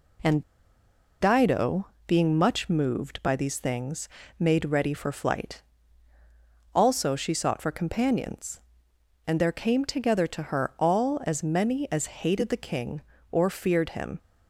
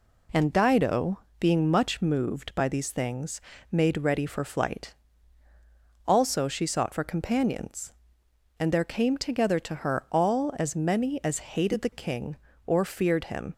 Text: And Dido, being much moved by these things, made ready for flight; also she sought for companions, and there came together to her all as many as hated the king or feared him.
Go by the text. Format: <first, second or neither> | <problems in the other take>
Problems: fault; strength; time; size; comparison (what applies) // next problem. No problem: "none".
second | pauses between "And" and "Dido"; noticeable; at 0.4 s; 0.78 s long